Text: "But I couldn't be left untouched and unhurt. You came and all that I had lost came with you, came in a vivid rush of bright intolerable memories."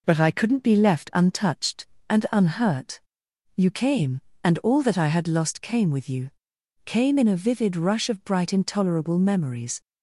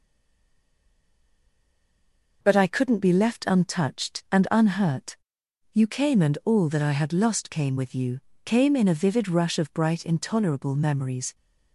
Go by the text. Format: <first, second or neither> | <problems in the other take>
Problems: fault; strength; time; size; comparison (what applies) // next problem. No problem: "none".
first | stays silent before the first word; until 2.4 s; 2.4 s long